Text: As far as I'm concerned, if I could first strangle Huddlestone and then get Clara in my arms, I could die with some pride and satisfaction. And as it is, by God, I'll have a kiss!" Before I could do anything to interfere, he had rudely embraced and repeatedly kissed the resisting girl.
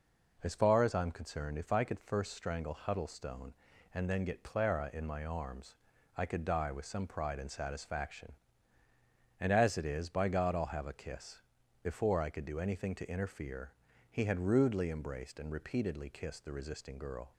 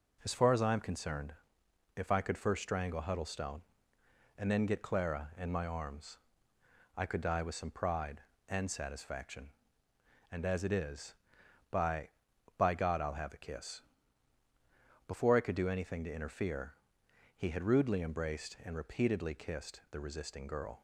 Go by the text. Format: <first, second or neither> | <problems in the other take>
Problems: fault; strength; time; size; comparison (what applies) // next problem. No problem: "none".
first | says "by" twice; at 12.5 s